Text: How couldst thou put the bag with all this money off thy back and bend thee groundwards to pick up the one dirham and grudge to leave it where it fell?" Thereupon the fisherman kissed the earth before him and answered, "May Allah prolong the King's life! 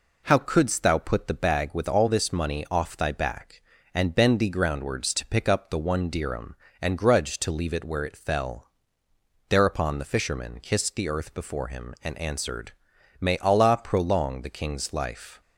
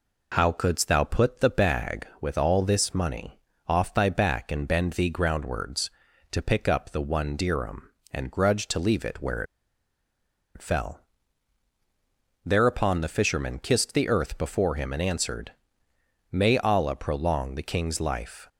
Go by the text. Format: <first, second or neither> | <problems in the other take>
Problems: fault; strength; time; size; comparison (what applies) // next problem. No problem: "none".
first | pauses between "money" and "off"; slight; at 3.3 s; 0.30 s long // pauses between "where" and "it"; at 9.4 s; 1.1 s long